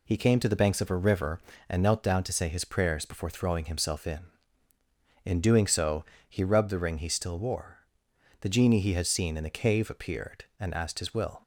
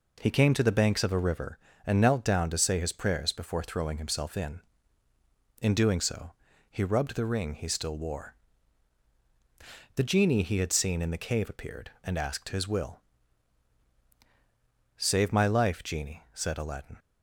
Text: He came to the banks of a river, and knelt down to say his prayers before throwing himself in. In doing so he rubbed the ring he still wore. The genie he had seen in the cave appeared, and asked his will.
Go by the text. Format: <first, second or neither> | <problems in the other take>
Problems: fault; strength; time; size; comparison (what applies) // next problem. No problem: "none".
first | pauses between "so" and "he"; at 6.3 s; 0.38 s long; slight in the first // goes on to say "Save my life genie said Aladdin"; strong; from 14.9 s on; 2.0 s long